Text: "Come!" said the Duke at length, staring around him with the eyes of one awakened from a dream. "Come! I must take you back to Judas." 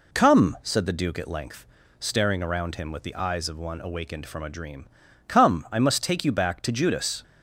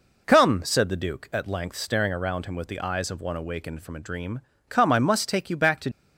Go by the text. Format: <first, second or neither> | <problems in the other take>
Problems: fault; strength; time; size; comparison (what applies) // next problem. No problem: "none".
first | stops before "Judas"; at 5.9 s